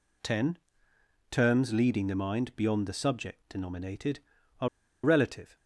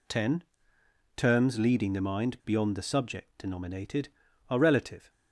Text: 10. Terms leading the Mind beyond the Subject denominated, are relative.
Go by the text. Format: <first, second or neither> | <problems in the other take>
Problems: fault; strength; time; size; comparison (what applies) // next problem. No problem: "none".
second | pauses between "are" and "relative"; slight; at 4.6 s; 0.36 s long